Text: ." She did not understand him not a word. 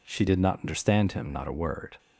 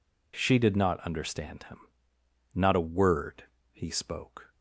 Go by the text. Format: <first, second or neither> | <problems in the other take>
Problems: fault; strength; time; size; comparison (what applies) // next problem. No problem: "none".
first | pauses between "him" and "not"; noticeable; at 1.8 s; 0.70 s long // goes on to say "He spoke"; noticeable; from 3.7 s on; 0.80 s long